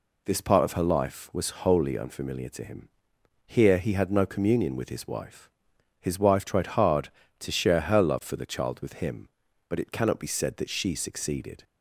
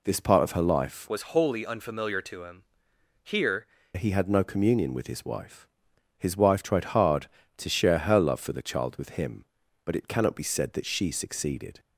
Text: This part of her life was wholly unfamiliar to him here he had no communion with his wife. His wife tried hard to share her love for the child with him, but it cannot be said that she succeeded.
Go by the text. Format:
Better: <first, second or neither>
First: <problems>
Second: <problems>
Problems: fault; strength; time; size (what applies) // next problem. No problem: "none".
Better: first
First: pauses between "him" and "here"; noticeable; at 2.8 s; 0.58 s long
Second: changes voice from "was" to "here"; from 1.0 to 3.6 s; 2.6 s long // pauses between "him" and "here"; noticeable; at 2.6 s; 0.60 s long